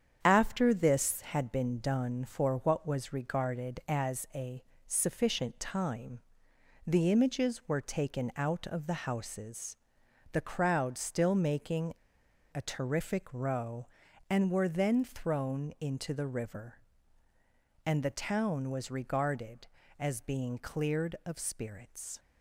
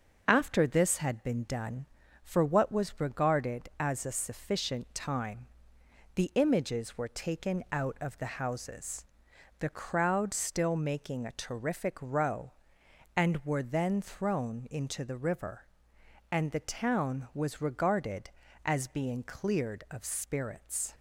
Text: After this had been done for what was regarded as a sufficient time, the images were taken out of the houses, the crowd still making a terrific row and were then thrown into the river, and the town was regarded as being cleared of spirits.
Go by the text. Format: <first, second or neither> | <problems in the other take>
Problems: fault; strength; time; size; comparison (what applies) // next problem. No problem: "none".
second | starts louder than the rest; strong; until 1.2 s; 8 dB; noticeable in the second // pauses between "a" and "sufficient"; slight; at 4.6 s; 0.24 s long // pauses between "making" and "a"; noticeable; at 11.9 s; 0.59 s long